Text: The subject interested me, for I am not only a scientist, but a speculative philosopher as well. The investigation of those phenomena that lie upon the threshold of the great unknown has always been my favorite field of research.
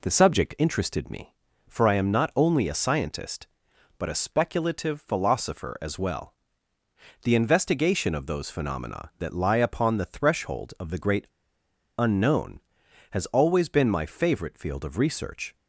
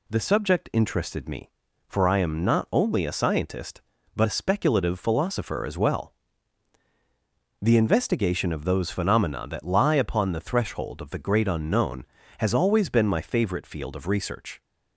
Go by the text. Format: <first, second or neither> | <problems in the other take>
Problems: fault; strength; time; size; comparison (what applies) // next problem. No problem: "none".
second | pauses between "great" and "unknown"; noticeable; at 11.2 s; 0.70 s long